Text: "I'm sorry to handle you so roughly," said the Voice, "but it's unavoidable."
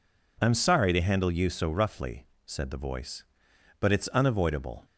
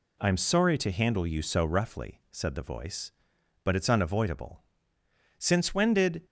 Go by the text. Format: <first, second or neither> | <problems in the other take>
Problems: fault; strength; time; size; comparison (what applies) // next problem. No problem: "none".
first | goes on to say "Since when did"; noticeable; from 5.3 s on; 0.86 s long